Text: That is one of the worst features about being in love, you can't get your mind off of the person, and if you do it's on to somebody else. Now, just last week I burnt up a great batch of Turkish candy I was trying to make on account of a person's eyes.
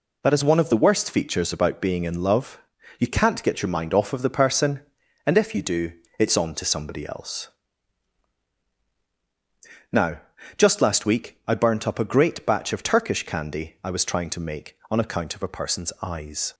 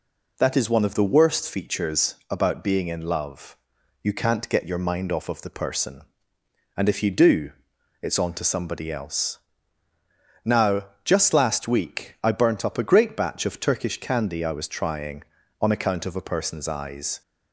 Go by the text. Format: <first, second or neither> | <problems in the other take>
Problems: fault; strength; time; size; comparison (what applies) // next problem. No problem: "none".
first | pauses between "do" and "it's"; noticeable; at 7.5 s; 0.50 s long; slight in the first // skips "to make"; at 15.4 s